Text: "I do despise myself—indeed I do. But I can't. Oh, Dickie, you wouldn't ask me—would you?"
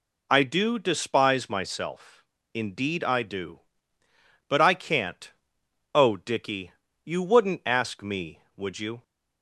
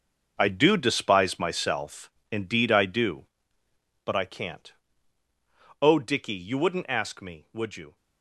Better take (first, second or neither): first